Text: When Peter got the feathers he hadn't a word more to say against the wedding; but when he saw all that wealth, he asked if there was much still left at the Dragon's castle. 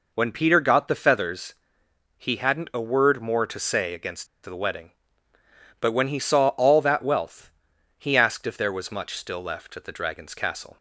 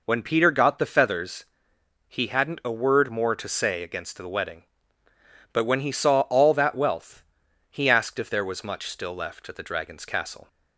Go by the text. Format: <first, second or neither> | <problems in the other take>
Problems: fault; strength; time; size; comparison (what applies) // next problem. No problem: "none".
second | pauses between "feathers" and "he"; noticeable; at 1.5 s; 0.64 s long; noticeable in the second // pauses between "against" and "the"; slight; at 4.2 s; 0.18 s long